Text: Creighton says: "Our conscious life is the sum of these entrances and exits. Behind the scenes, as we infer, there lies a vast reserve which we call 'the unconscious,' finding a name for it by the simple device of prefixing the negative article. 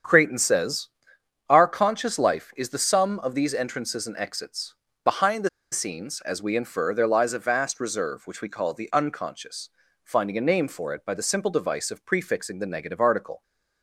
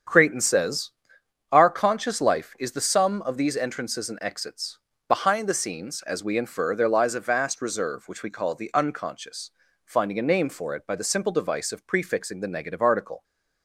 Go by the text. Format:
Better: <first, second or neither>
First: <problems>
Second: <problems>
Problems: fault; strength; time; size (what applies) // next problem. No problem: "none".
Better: second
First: starts louder than the rest; strong; until 1.6 s; 8 dB // pauses between "the" and "scenes"; slight; at 5.4 s; 0.22 s long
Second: starts louder than the rest; strong; until 1.7 s; 8 dB